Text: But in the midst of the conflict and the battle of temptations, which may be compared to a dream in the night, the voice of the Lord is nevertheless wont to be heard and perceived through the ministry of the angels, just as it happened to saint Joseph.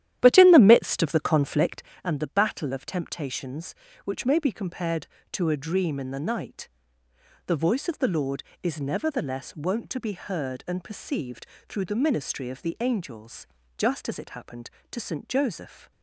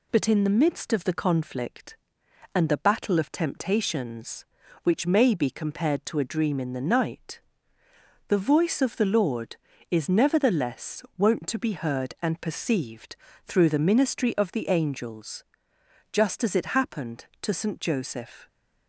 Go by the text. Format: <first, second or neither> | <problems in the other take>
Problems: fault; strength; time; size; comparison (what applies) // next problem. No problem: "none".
second | starts louder than the rest; strong; until 2.0 s; 12 dB // pauses between "perceived" and "through"; slight; at 11.4 s; 0.24 s long; slight in the second